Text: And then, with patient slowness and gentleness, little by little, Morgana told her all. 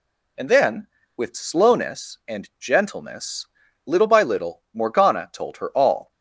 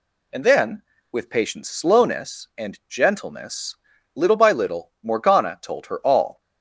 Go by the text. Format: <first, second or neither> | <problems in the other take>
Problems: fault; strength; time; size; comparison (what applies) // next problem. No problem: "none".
second | skips "patient"; at 1.3 s